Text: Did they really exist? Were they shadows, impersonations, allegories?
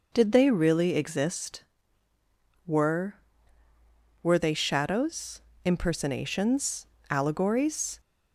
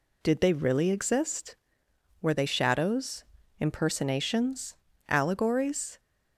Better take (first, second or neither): second